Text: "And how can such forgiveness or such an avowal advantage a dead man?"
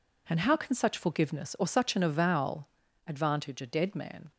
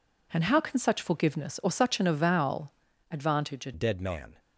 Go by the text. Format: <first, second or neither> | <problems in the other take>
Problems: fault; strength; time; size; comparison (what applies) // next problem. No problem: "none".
first | pauses between "avowal" and "advantage"; at 2.7 s; 0.38 s long; also in the first // changes voice at "dead"; from 3.7 s on; 0.6 s long